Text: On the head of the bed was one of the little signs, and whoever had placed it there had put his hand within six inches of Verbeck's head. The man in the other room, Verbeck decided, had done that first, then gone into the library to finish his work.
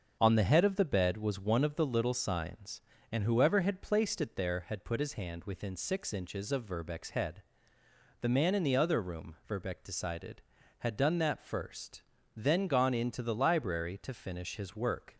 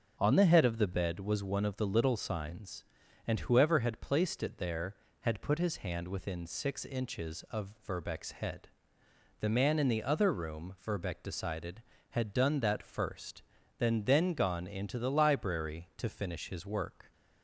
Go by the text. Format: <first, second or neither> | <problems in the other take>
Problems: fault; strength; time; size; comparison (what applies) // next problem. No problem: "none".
first | starts louder than the rest; until 1.2 s; 7 dB; also in the first // says "then" twice; at 14.0 s